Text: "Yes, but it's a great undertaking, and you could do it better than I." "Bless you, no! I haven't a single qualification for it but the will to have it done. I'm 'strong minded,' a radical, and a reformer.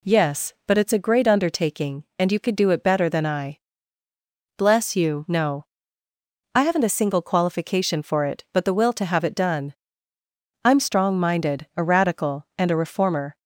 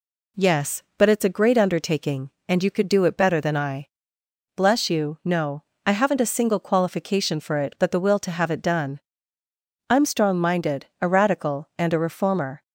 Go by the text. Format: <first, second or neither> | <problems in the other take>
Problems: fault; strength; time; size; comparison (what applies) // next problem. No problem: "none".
neither | none